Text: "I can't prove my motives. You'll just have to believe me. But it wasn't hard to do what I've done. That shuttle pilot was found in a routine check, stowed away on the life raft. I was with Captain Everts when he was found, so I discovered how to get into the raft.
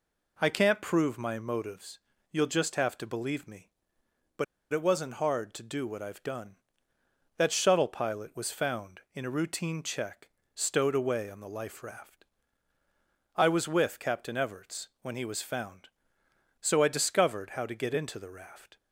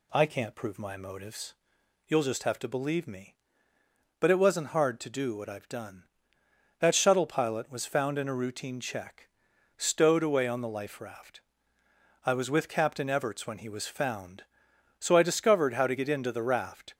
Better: second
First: pauses between "But" and "it"; slight; at 4.4 s; 0.28 s long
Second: none

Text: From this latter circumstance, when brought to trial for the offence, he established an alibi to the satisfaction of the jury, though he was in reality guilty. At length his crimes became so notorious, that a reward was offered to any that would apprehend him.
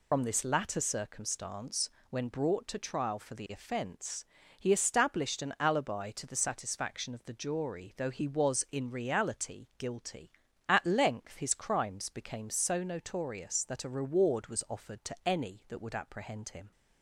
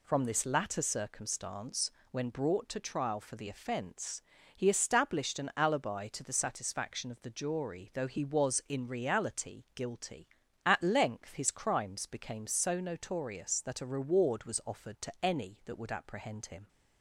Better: second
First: loses the start of "From"; at 0.1 s; 75 ms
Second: none

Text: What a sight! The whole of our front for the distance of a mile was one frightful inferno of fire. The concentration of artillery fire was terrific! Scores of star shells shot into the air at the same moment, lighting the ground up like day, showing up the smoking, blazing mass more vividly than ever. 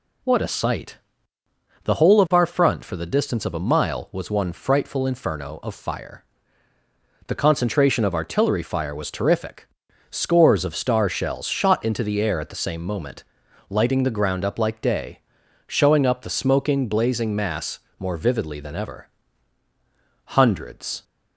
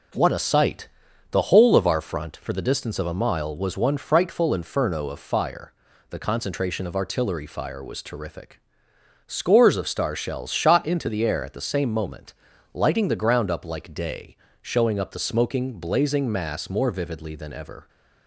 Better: second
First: pauses between "mass" and "more"; slight; at 17.7 s; 0.20 s long // goes on to say "Hundreds"; noticeable; from 20.2 s on; 0.78 s long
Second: none

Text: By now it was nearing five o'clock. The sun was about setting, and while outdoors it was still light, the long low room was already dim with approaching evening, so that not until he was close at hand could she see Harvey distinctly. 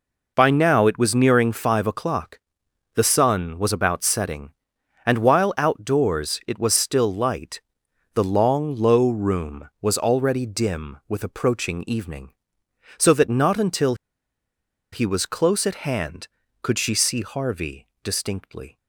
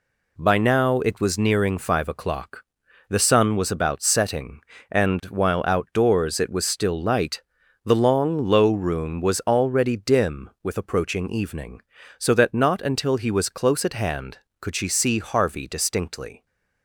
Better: second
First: pauses between "until" and "he"; at 13.9 s; 0.98 s long // pauses between "Harvey" and "distinctly"; slight; at 17.8 s; 0.16 s long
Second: none

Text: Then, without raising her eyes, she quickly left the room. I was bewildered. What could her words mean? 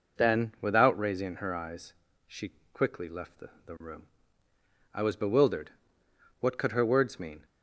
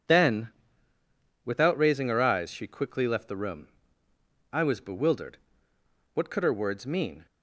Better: second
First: pauses between "she" and "quickly"; slight; at 2.5 s; 0.18 s long // says "the" twice; at 3.6 s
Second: none

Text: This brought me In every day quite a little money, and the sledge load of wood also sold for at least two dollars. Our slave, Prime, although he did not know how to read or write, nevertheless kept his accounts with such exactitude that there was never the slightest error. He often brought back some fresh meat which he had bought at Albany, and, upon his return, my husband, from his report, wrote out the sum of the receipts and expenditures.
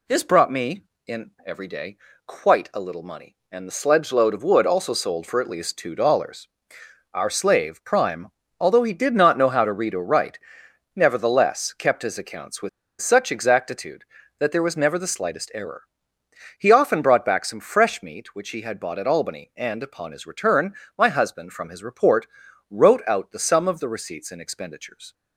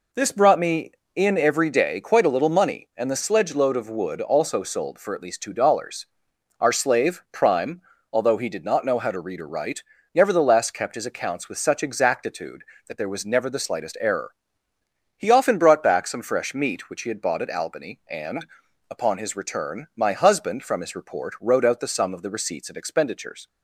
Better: second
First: pauses between "day" and "quite"; slight; at 1.9 s; 0.30 s long // pauses between "with" and "such"; slight; at 12.6 s; 0.31 s long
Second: none

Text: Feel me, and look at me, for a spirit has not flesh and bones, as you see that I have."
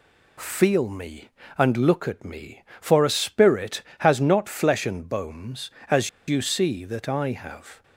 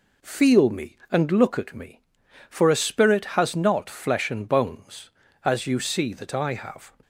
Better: second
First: pauses between "as" and "you"; slight; at 6.0 s; 0.19 s long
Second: none

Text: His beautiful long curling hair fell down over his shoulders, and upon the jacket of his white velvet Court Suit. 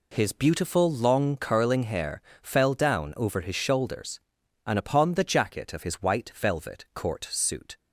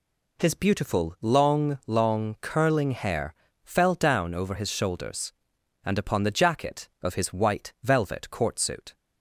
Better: first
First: pauses between "hair" and "fell"; slight; at 2.2 s; 0.22 s long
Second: says "long" twice; at 1.8 s // pauses between "hair" and "fell"; slight; at 3.3 s; 0.30 s long

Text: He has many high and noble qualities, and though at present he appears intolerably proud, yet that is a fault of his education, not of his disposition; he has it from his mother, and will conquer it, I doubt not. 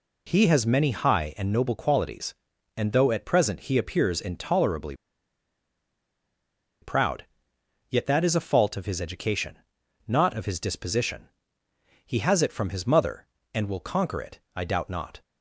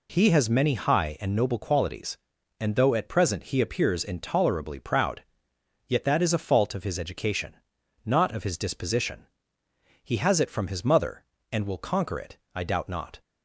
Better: second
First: pauses between "intolerably" and "proud"; strong; at 4.9 s; 1.8 s long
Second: none

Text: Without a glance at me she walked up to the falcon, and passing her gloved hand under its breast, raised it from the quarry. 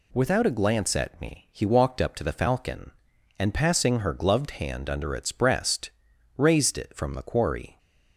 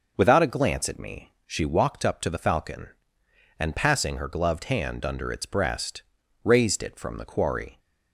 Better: second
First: says "he" for "she"; at 1.5 s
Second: none

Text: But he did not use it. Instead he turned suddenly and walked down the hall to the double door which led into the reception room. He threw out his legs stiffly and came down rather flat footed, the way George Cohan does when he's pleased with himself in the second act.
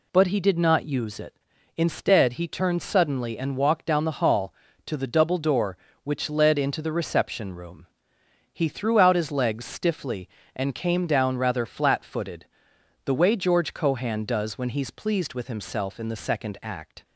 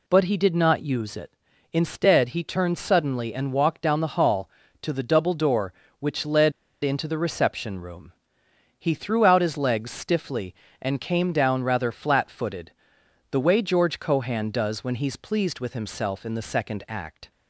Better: first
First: none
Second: pauses between "led" and "into"; slight; at 6.5 s; 0.32 s long

